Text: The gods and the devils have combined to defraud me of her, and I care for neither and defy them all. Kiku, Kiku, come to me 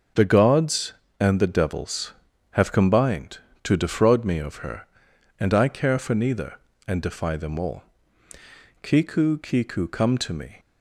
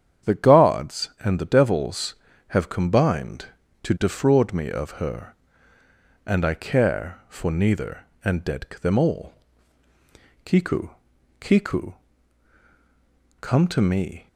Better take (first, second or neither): first